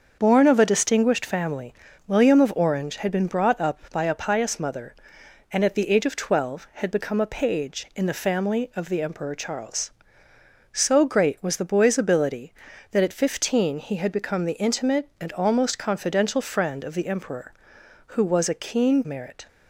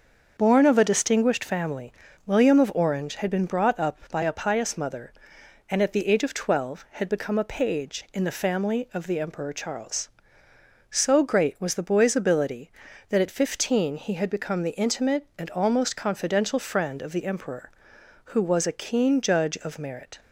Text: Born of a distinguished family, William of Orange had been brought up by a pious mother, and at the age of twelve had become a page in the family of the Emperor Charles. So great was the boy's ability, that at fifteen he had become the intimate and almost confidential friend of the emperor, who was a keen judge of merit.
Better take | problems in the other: second | starts louder than the rest; until 1.2 s; 6.5 dB; also in the second // skips "judge of"; at 19.0 s

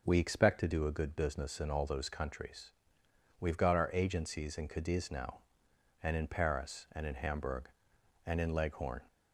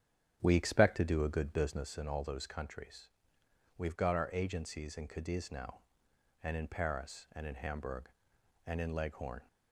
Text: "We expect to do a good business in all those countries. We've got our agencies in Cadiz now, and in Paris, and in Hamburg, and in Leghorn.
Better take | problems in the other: first | starts louder than the rest; strong; until 1.9 s; 9.5 dB

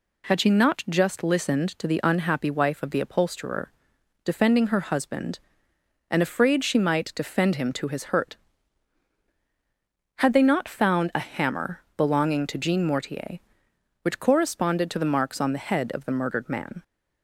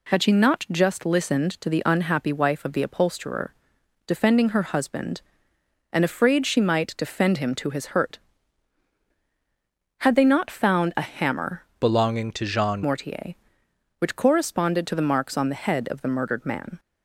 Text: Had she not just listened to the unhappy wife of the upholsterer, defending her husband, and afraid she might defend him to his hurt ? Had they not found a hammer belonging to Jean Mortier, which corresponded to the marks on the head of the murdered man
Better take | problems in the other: first | changes voice from "belonging" to "Jean"; from 11.7 to 12.8 s; 1.1 s long

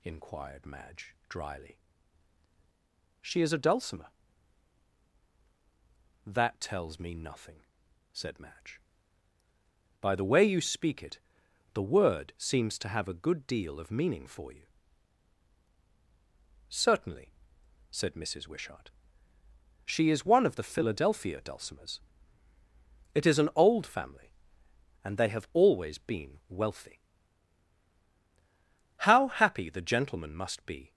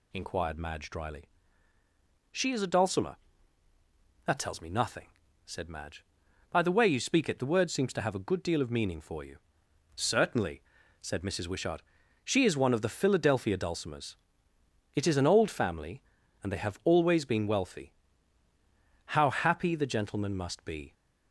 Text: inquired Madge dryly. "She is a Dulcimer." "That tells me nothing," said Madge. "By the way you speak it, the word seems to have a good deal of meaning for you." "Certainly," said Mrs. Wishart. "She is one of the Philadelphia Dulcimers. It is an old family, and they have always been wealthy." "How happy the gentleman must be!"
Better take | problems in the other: neither | none

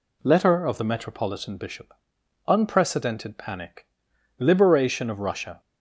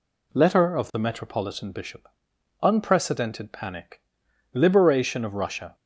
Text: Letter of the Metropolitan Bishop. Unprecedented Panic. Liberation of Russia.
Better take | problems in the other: neither | none

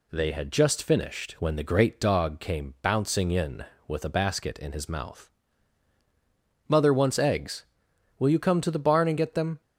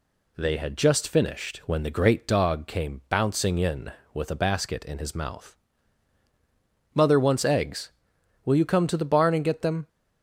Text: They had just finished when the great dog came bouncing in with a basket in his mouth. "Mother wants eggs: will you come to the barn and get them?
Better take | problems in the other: neither | none

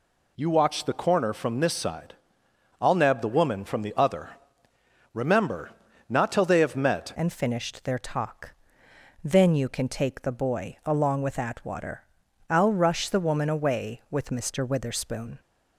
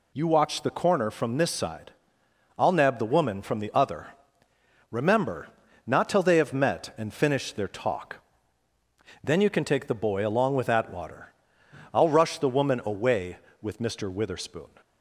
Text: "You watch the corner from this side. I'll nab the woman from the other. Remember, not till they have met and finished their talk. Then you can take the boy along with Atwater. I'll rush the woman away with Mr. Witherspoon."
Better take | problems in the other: second | changes voice at "and"; from 7.1 s on; 8.2 s long

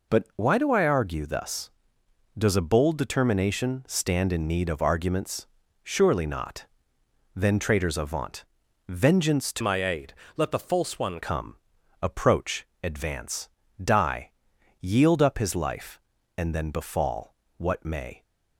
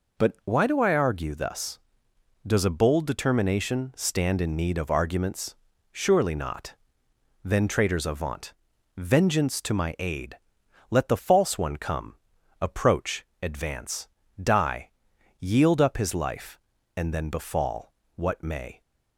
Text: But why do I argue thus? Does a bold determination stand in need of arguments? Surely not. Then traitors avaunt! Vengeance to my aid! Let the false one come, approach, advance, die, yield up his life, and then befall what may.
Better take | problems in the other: second | changes voice from "my" to "one"; from 9.6 to 11.2 s; 1.6 s long // pauses between "befall" and "what"; slight; at 17.3 s; 0.24 s long; slight in the second

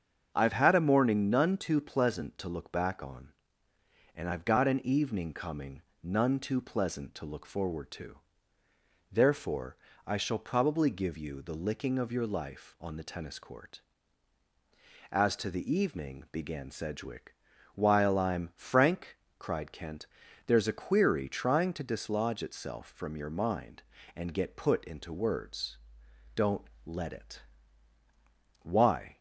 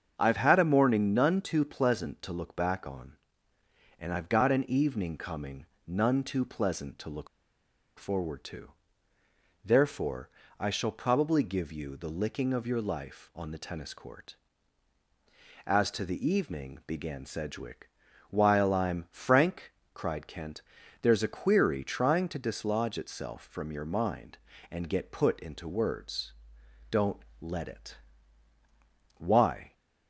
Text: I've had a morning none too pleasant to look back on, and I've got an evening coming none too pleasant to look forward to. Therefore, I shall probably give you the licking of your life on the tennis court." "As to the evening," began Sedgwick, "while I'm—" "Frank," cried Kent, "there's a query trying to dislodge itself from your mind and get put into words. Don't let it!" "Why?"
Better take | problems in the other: first | starts louder than the rest; until 1.1 s; 7 dB; also in the first // pauses between "coming" and "none"; slight; at 5.6 s; 0.22 s long; slight in the first // pauses between "look" and "forward"; noticeable; at 7.2 s; 0.71 s long // pauses between "Don't" and "let"; slight; at 27.2 s; 0.16 s long; slight in the first

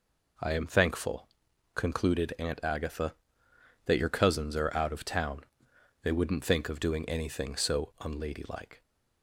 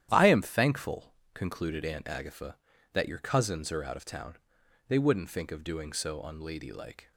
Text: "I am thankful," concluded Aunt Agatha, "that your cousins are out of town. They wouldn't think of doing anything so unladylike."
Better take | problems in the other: first | starts louder than the rest; strong; until 1.1 s; 11 dB // skips "anything"; at 5.9 s

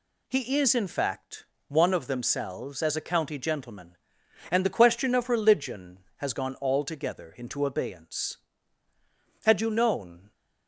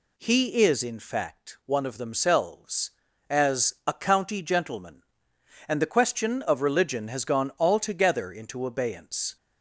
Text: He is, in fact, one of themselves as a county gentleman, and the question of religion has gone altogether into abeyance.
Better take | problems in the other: second | goes on to say "Had you known"; noticeable; from 9.4 s on; 0.88 s long

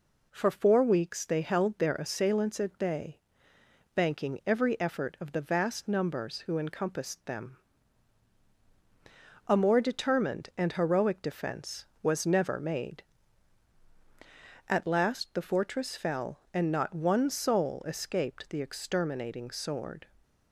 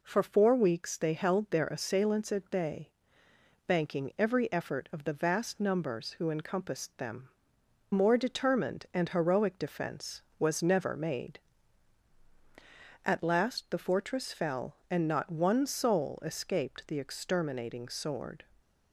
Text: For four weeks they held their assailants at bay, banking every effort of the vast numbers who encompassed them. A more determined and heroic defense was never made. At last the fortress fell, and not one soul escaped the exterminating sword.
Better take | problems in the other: first | skips "A"; at 7.6 s

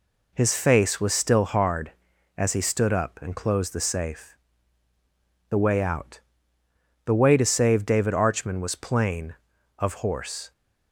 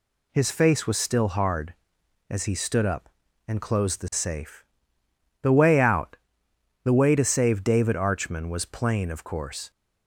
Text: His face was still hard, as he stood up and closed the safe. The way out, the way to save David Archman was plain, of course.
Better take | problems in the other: second | says "horse" for "course"; at 9.9 s

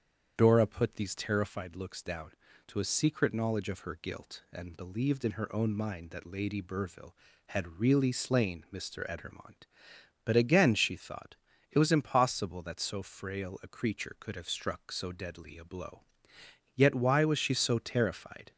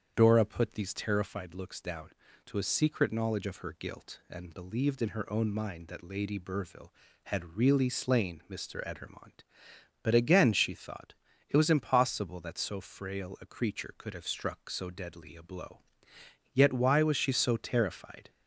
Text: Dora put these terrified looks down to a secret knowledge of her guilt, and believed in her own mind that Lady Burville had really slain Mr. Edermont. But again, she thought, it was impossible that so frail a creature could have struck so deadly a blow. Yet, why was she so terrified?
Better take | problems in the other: neither | starts louder than the rest; strong; the same in both

